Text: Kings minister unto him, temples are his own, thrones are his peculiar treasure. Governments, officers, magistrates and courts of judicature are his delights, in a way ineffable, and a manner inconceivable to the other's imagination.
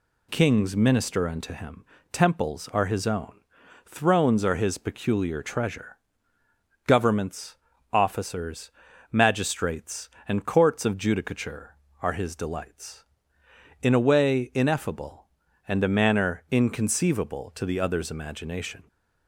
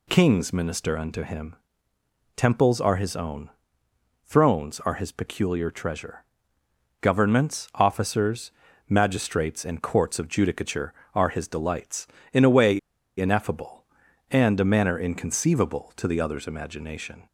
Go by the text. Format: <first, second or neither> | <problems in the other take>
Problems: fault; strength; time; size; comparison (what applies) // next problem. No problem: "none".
first | pauses between "way" and "ineffable"; at 12.7 s; 0.38 s long